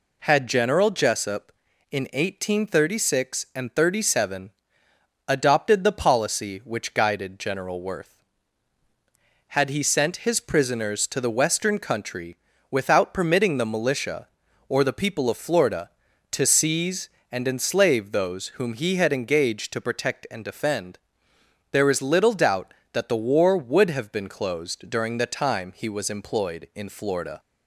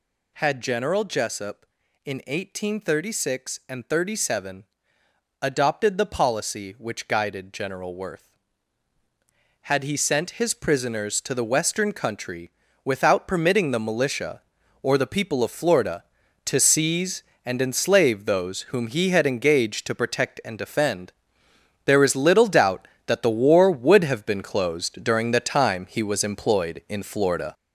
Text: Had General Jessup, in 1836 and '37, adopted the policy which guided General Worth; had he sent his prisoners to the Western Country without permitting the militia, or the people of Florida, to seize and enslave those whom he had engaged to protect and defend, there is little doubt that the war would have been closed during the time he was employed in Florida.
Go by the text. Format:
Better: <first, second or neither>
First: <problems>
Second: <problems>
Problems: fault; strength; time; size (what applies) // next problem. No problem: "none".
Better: first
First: pauses between "Country" and "without"; slight; at 12.3 s; 0.34 s long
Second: gets louder; noticeable; throughout; 5.5 dB // pauses between "Country" and "without"; slight; at 12.4 s; 0.34 s long